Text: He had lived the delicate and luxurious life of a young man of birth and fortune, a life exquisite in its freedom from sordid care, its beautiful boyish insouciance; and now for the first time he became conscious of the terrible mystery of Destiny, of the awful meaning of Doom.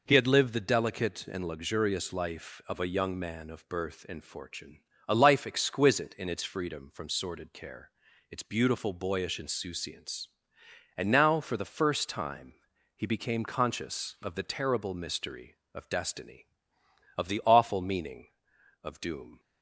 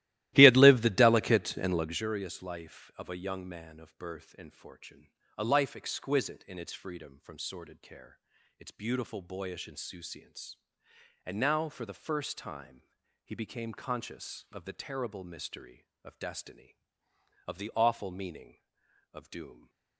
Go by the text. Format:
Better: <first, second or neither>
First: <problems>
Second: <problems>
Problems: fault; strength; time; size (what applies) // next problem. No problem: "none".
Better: first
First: pauses between "time" and "he"; at 12.5 s; 0.42 s long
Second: starts louder than the rest; strong; until 2.1 s; 16 dB // pauses between "time" and "he"; at 12.8 s; 0.42 s long